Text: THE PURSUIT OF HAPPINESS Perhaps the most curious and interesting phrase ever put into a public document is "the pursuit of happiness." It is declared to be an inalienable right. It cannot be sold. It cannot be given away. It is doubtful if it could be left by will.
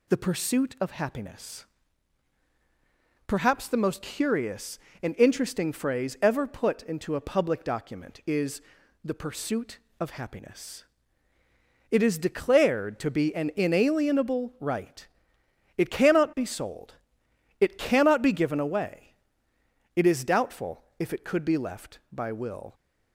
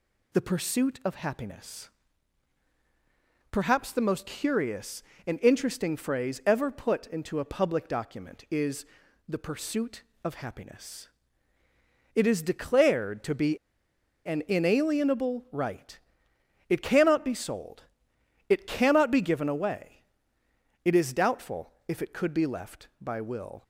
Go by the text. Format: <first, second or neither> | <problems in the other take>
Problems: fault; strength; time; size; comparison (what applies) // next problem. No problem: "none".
first | pauses between "HAPPINESS" and "Perhaps"; strong; at 1.8 s; 1.6 s long; strong in the first // pauses between "is" and "the"; at 8.8 s; 0.42 s long; also in the first // pauses between "be" and "an"; noticeable; at 13.5 s; 0.69 s long // pauses between "doubtful" and "if"; slight; at 21.7 s; 0.16 s long; slight in the first